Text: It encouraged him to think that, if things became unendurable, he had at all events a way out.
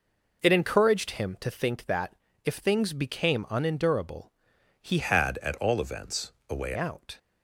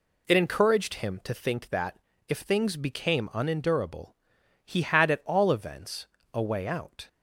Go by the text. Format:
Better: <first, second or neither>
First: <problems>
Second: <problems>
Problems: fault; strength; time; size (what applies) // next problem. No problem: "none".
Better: second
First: changes voice from "had" to "way"; from 5.0 to 6.7 s; 1.7 s long // pauses between "events" and "a"; slight; at 6.2 s; 0.18 s long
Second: pauses between "events" and "a"; slight; at 6.0 s; 0.26 s long